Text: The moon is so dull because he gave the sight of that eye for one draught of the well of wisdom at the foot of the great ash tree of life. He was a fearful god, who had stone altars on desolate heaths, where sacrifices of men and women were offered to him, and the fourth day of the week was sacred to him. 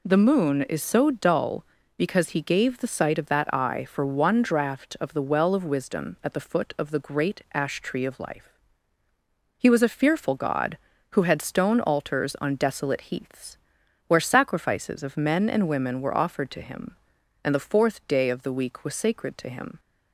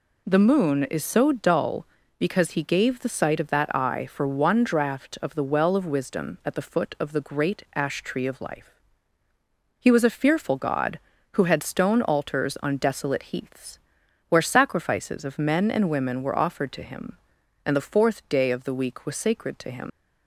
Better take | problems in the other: first | leaves "him" unfinished; at 19.8 s; 110 ms

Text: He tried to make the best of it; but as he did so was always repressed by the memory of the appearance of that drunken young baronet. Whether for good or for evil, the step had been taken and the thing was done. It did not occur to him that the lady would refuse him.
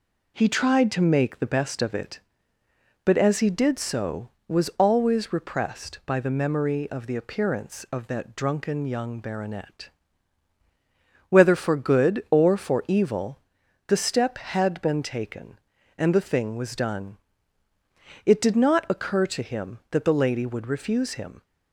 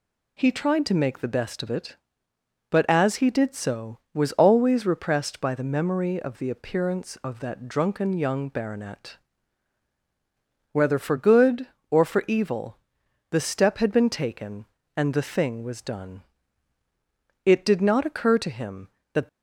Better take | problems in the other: first | stops before "the lady would refuse him"; at 19.2 s

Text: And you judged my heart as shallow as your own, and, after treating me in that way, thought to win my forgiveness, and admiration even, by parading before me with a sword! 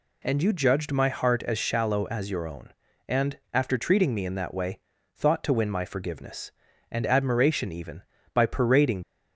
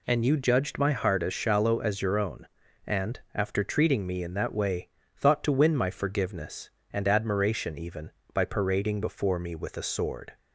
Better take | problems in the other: second | stops before "before me with a sword"; at 9.0 s

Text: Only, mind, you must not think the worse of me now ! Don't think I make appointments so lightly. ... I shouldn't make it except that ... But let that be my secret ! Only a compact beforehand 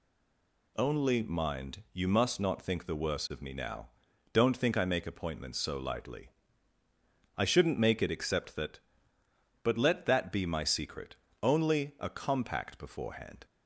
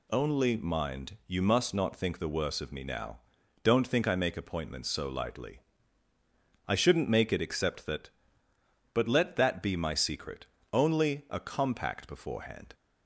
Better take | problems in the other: second | stays silent before the first word; slight; until 0.7 s; 0.7 s long

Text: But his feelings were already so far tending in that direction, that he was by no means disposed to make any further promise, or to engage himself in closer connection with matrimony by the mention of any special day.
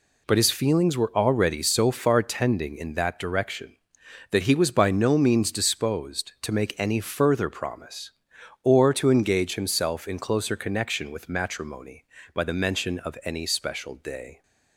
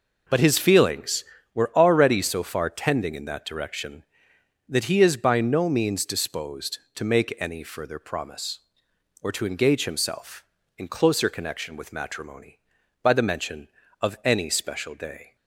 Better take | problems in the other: first | says "is" for "was"; at 4.9 s

